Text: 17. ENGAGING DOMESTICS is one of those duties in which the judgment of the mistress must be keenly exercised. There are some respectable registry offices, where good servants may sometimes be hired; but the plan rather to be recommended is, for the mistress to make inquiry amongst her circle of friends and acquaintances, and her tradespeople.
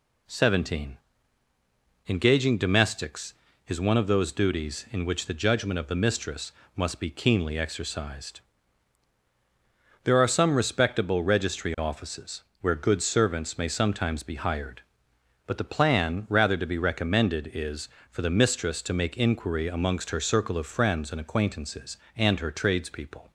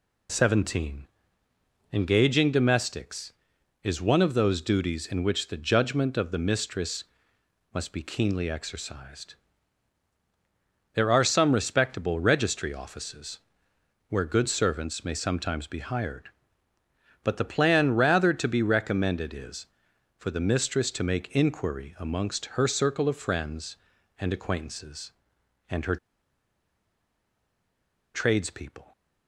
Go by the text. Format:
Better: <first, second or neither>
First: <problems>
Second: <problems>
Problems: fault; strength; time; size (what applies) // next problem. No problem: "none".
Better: first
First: pauses between "mistress" and "must"; slight; at 6.5 s; 0.24 s long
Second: pauses between "mistress" and "must"; noticeable; at 7.0 s; 0.72 s long // pauses between "her" and "tradespeople"; strong; at 25.9 s; 2.1 s long